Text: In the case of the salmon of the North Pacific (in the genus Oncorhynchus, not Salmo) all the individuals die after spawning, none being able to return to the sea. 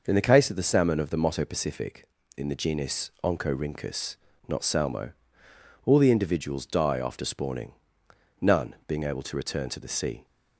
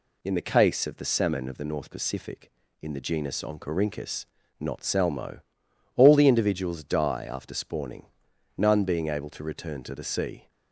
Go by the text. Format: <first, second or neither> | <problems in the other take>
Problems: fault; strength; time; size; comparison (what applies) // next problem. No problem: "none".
second | says "Motto" for "North"; at 1.2 s